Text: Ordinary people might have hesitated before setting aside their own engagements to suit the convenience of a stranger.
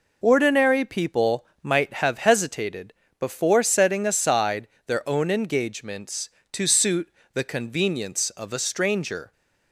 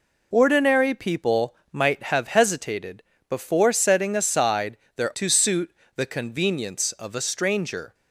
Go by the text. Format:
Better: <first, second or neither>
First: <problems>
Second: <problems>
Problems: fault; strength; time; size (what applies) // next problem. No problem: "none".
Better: first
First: pauses between "people" and "might"; slight; at 1.4 s; 0.20 s long // pauses between "hesitated" and "before"; slight; at 2.9 s; 0.26 s long // pauses between "aside" and "their"; slight; at 4.6 s; 0.18 s long // pauses between "suit" and "the"; slight; at 7.0 s; 0.24 s long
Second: pauses between "people" and "might"; slight; at 1.5 s; 0.20 s long // pauses between "hesitated" and "before"; slight; at 3.0 s; 0.26 s long // pauses between "aside" and "their"; slight; at 4.7 s; 0.18 s long // skips "own engagements"; at 5.1 s // pauses between "suit" and "the"; slight; at 5.7 s; 0.24 s long